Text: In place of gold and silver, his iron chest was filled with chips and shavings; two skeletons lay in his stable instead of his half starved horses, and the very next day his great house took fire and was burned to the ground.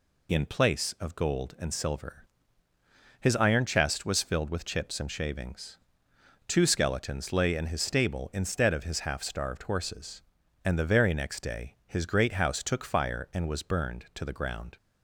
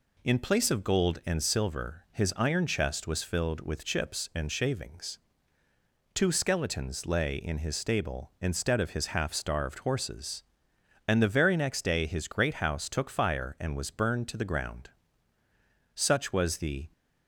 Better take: first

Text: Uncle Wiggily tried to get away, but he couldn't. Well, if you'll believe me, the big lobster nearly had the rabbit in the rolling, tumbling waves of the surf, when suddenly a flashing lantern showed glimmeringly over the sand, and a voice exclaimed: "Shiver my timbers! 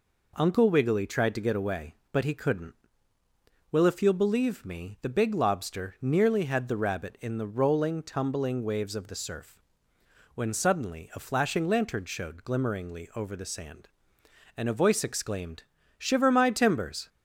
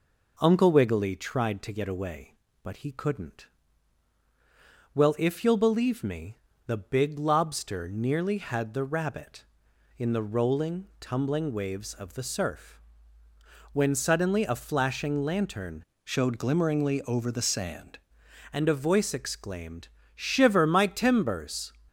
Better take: first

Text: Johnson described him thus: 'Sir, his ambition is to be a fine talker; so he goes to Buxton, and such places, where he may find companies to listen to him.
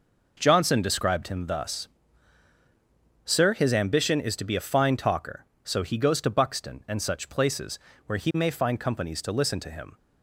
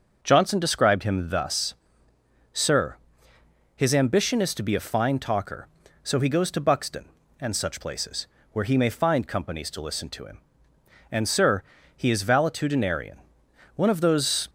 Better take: first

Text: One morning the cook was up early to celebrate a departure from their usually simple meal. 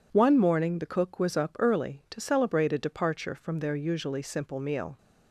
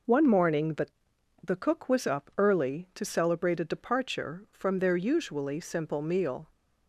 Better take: first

